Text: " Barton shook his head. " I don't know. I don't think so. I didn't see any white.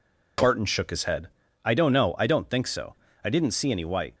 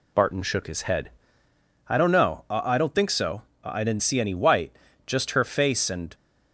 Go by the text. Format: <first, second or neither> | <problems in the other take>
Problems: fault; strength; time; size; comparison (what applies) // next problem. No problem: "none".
first | goes on to say "Just her face and"; noticeable; from 5.0 s on; 1.0 s long